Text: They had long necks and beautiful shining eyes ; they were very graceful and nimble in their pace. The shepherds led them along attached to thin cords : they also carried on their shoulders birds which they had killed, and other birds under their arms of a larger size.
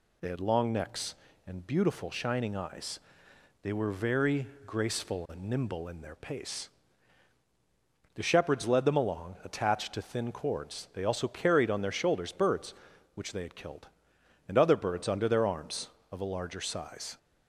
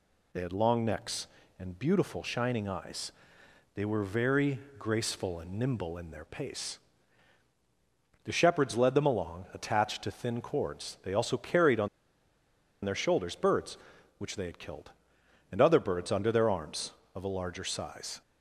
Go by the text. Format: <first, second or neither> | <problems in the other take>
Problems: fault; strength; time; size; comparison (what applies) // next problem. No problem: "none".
first | pauses between "very" and "graceful"; slight; at 4.5 s; 0.20 s long; slight in the first // pauses between "on" and "their"; noticeable; at 11.8 s; 0.96 s long